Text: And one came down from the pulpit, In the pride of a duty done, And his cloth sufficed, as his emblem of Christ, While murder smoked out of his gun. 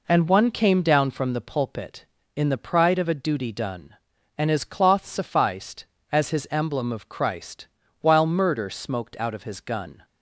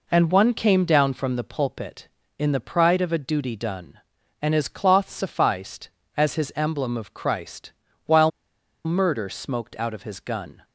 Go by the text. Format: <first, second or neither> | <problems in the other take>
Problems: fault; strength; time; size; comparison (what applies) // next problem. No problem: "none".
first | pauses between "While" and "murder"; noticeable; at 8.3 s; 0.55 s long